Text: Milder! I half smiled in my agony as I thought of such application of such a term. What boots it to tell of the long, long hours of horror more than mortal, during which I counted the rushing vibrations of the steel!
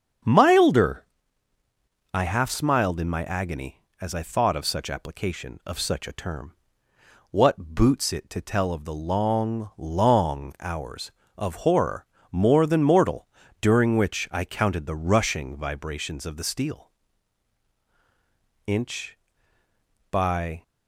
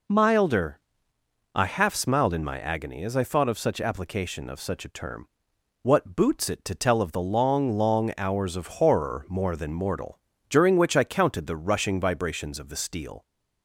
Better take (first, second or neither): second